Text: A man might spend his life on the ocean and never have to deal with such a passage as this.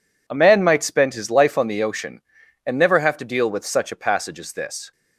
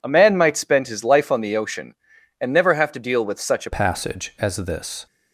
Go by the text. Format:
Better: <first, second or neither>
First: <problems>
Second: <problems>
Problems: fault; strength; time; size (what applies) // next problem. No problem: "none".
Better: first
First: none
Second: changes voice at "passage"; from 3.7 s on; 1.3 s long